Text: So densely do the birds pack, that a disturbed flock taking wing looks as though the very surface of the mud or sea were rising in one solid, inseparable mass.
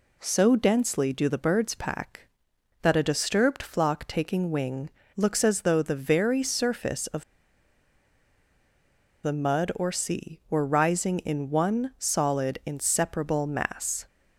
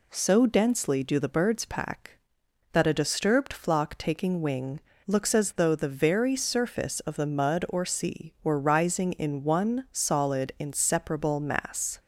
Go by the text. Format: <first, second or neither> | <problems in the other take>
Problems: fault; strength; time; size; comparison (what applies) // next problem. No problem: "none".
second | pauses between "wing" and "looks"; slight; at 4.8 s; 0.26 s long; slight in the second // pauses between "of" and "the"; strong; at 7.2 s; 1.9 s long